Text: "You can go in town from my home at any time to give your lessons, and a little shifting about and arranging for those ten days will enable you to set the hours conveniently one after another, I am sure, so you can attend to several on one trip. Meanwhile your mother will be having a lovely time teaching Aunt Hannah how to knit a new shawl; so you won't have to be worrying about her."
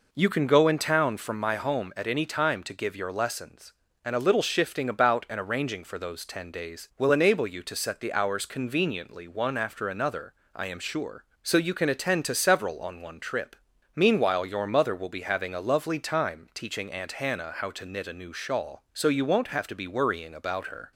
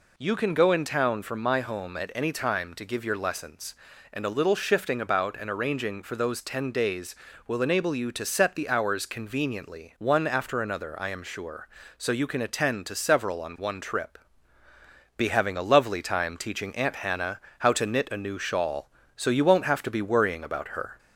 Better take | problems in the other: first | skips "Meanwhile your mother will"; at 14.6 s // pauses between "Hannah" and "how"; slight; at 17.4 s; 0.16 s long

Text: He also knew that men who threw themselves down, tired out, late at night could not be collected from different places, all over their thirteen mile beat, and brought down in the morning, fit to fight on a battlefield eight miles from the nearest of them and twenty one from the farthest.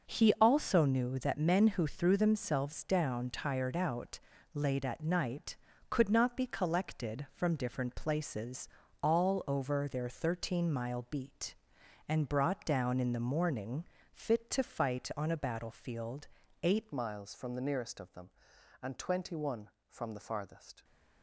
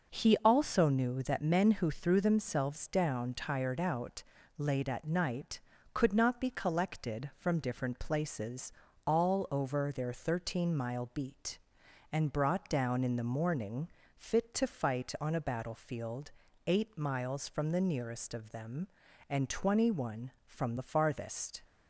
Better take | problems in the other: second | pauses between "battlefield" and "eight"; slight; at 16.2 s; 0.34 s long; slight in the second // changes voice at "miles"; from 16.9 s on; 3.9 s long

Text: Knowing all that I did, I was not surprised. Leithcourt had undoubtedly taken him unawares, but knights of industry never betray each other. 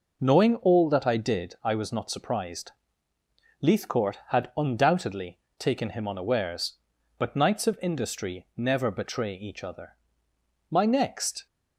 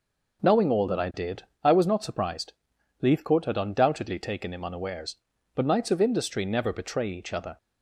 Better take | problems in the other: second | pauses between "undoubtedly" and "taken"; slight; at 5.3 s; 0.20 s long // goes on to say "My next"; noticeable; from 10.7 s on; 0.76 s long

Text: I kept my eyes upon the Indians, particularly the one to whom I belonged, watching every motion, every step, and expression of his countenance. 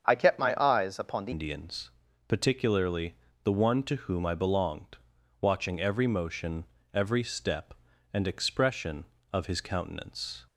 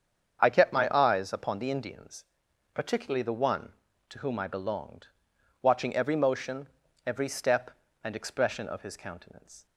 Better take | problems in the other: second | starts louder than the rest; strong; until 1.1 s; 7.5 dB; strong in the second // changes voice at "Indians"; from 1.3 s on; 9.1 s long // pauses between "particularly" and "the"; slight; at 3.1 s; 0.26 s long

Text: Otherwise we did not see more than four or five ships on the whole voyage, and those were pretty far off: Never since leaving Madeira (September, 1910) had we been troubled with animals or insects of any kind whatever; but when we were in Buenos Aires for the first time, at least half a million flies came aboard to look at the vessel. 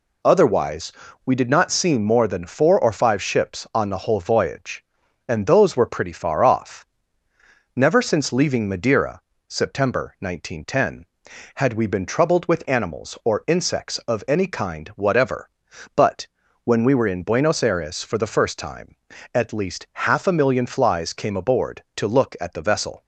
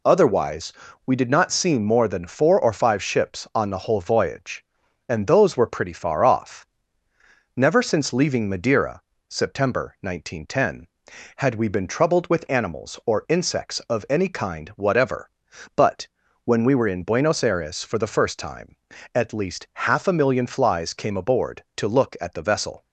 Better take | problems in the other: neither | pauses between "Otherwise" and "we"; slight; the same in both // pauses between "but" and "when"; the same in both

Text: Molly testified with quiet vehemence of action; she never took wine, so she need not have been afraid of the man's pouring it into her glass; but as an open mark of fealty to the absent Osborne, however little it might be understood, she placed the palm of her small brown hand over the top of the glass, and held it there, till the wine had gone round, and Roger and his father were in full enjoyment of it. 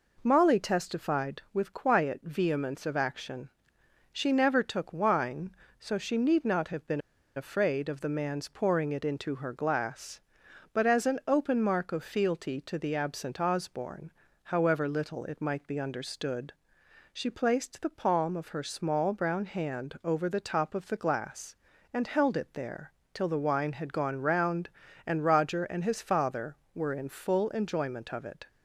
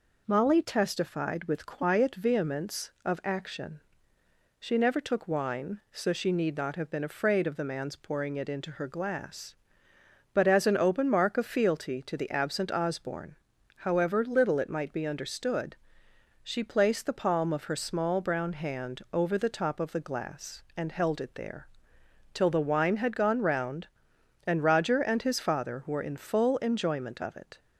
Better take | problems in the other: second | pauses between "been" and "afraid"; at 6.9 s; 0.37 s long

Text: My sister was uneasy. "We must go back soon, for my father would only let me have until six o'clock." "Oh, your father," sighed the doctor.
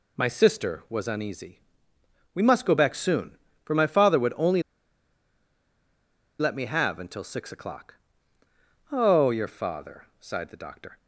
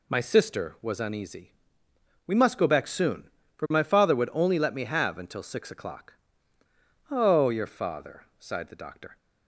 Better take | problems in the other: second | pauses between "only" and "let"; strong; at 4.6 s; 1.7 s long

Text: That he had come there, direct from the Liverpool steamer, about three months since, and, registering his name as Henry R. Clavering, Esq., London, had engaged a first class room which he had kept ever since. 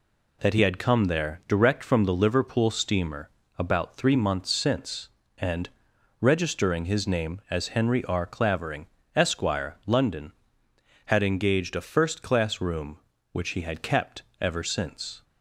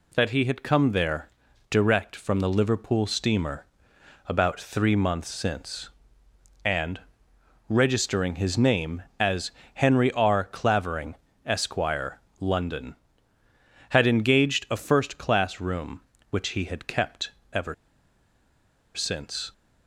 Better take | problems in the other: first | pauses between "as" and "Henry"; slight; at 9.5 s; 0.24 s long // pauses between "kept" and "ever"; slight; at 17.3 s; 0.22 s long; slight in the first // pauses between "ever" and "since"; at 17.7 s; 1.2 s long

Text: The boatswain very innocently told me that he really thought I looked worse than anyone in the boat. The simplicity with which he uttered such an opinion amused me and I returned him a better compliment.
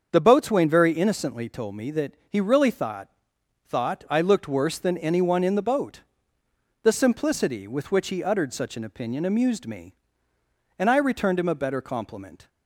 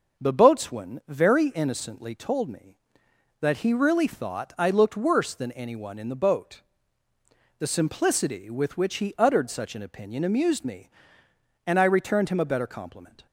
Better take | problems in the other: second | starts louder than the rest; until 1.1 s; 7 dB // pauses between "that" and "he"; slight; at 2.1 s; 0.16 s long // says "thought" twice; at 3.6 s

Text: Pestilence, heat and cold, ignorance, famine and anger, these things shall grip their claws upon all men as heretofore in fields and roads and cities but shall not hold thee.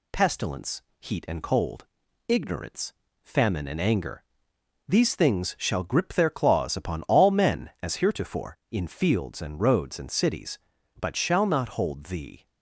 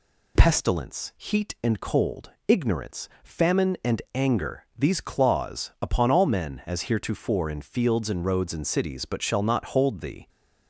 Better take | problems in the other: first | skips "things shall grip their"; at 5.0 s

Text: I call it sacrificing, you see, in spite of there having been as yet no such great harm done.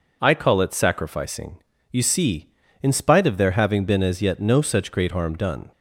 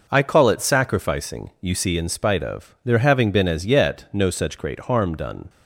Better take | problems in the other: neither | none

